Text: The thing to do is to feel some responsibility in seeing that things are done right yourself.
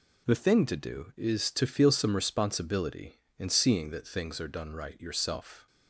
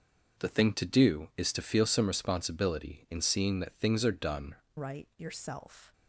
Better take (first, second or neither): first